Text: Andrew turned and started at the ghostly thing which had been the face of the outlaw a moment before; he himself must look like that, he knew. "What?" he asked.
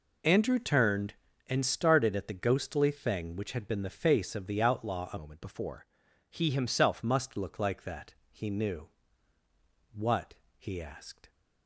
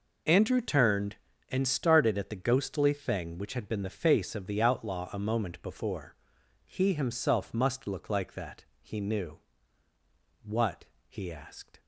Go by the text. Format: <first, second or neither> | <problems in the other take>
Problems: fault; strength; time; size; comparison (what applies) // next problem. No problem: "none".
second | changes voice from "moment" to "himself"; from 5.1 to 7.0 s; 1.9 s long